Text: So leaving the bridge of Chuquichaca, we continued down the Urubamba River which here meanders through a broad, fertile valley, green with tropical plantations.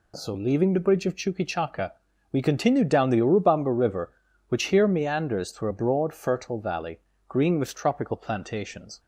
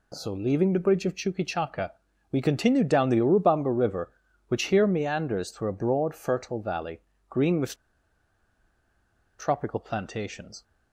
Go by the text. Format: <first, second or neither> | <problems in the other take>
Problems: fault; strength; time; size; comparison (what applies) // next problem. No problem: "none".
first | pauses between "with" and "tropical"; strong; at 7.7 s; 1.6 s long